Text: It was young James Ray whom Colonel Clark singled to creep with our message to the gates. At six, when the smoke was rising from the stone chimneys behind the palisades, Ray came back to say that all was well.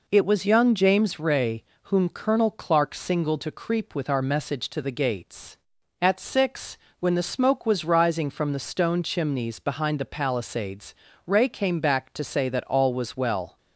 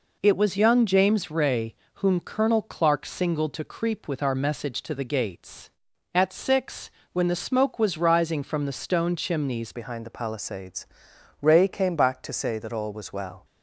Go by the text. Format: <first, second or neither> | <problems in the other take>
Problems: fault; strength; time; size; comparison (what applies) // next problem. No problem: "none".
first | pauses between "Ray" and "whom"; slight; at 1.7 s; 0.18 s long; slight in the first // changes voice at "behind"; from 9.7 s on; 3.7 s long